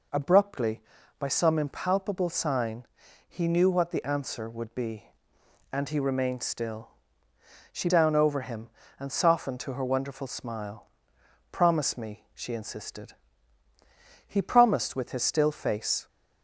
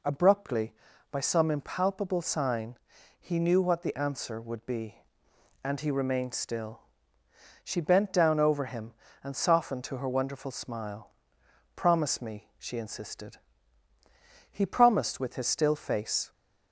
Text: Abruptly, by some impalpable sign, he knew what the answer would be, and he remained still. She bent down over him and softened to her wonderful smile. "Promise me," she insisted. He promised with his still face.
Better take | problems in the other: second | skips "bent"; at 7.8 s

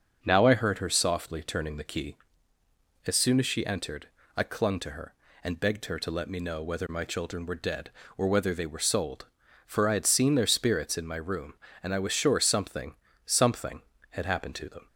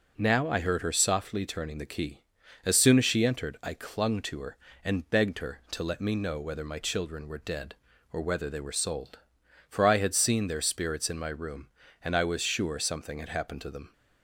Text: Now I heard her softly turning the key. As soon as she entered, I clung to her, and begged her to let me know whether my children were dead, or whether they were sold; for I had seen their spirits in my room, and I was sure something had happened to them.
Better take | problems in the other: second | starts louder than the rest; until 1.2 s; 6 dB // says "something" twice; at 13.2 s

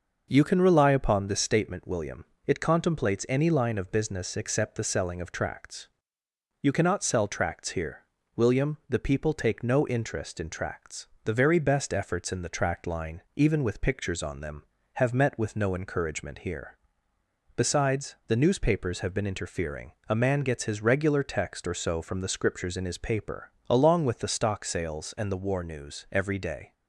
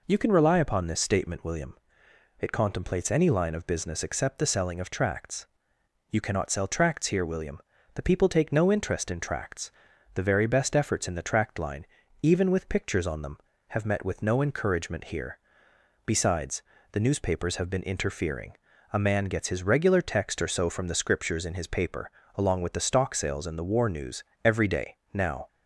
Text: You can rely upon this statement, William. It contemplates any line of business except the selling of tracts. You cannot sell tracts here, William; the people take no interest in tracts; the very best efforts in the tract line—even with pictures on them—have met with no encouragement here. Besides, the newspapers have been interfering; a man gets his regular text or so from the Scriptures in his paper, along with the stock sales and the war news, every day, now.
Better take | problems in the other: second | starts louder than the rest; noticeable; until 1.3 s; 6 dB // stops before "now"; at 26.7 s

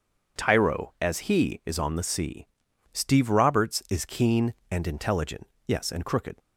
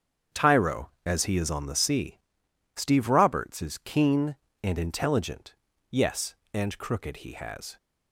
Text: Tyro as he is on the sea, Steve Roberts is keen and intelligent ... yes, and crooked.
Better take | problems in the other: first | starts louder than the rest; strong; until 1.4 s; 7.5 dB // goes on to say "He has"; from 7.1 s on; 0.60 s long

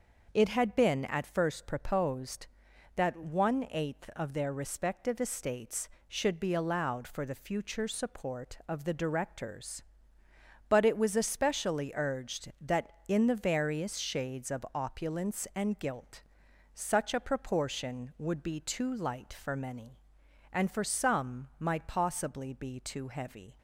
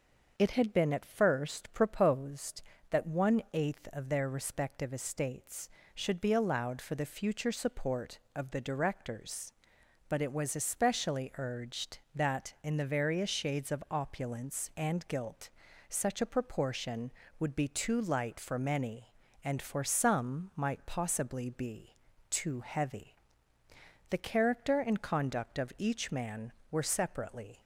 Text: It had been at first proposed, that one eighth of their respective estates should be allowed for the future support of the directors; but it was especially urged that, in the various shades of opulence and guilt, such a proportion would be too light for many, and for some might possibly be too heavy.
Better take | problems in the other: first | starts louder than the rest; until 1.3 s; 6.5 dB // pauses between "be" and "too"; slight; at 21.9 s; 0.34 s long // goes on to say "The character and conduct of each man were separately"; strong; from 24.1 s on; 3.5 s long

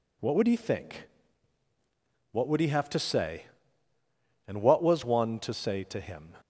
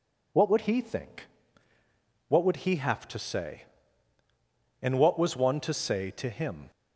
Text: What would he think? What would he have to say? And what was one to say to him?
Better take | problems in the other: neither | none

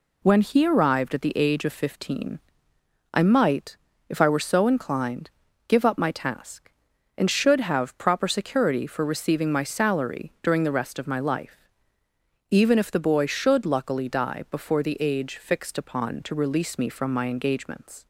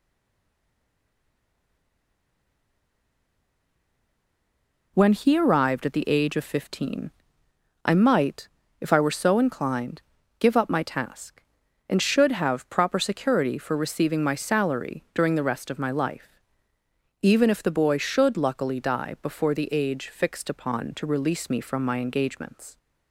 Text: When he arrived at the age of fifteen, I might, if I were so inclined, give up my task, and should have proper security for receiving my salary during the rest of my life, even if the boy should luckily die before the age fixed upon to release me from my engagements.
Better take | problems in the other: first | stays silent before the first word; strong; until 4.9 s; 4.9 s long

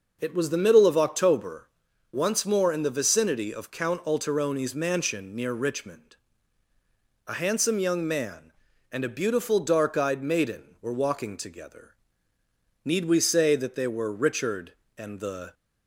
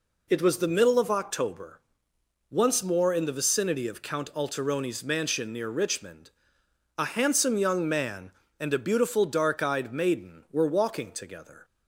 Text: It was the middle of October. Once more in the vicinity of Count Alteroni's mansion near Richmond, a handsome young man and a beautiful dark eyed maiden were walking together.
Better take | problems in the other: second | goes on to say "Need we say that they were Richard and the"; strong; from 12.8 s on; 2.7 s long

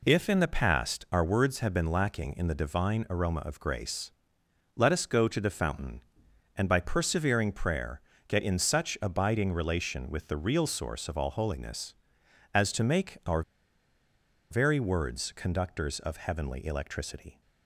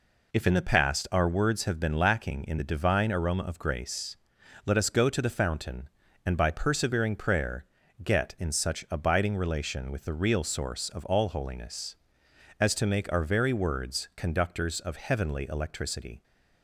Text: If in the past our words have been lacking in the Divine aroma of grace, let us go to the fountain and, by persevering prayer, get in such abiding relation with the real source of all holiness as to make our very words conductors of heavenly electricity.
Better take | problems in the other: second | pauses between "our" and "very"; at 13.4 s; 1.0 s long

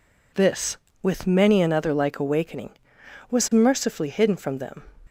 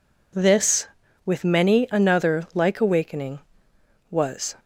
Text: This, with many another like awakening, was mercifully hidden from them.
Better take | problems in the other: first | stops before "mercifully hidden from them"; at 4.5 s

